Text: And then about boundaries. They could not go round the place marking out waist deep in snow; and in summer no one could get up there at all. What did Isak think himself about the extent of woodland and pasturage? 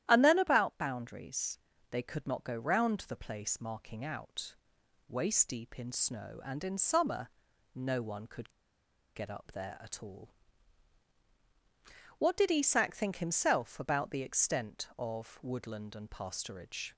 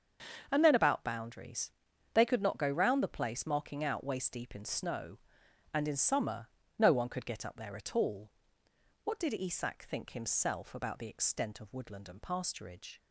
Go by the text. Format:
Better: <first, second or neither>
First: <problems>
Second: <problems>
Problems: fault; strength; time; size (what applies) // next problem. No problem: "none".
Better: second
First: starts louder than the rest; strong; until 1.0 s; 12 dB // pauses between "out" and "waist"; noticeable; at 4.5 s; 0.54 s long // pauses between "summer" and "no"; noticeable; at 7.2 s; 0.46 s long // pauses between "could" and "get"; noticeable; at 8.4 s; 0.66 s long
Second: starts louder than the rest; until 1.5 s; 6.5 dB // pauses between "summer" and "no"; slight; at 6.4 s; 0.30 s long